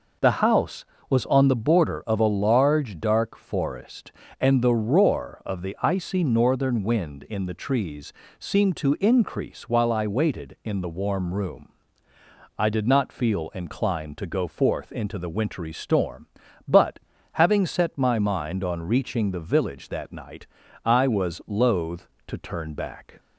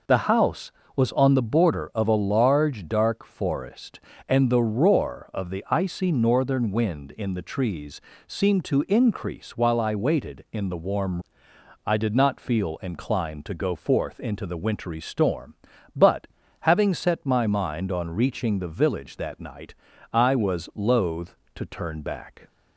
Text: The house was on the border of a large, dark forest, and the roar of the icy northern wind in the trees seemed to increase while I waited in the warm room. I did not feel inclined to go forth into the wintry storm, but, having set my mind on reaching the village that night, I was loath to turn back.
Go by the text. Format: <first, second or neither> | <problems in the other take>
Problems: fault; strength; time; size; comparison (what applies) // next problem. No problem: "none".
first | pauses between "trees" and "seemed"; slight; at 8.0 s; 0.26 s long; slight in the first // skips "room"; at 11.5 s